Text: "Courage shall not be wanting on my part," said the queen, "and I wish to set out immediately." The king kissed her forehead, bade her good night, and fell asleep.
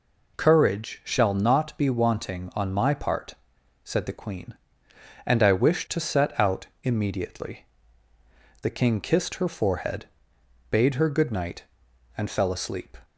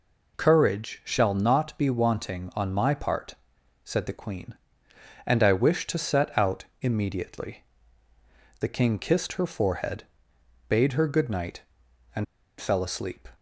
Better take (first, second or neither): first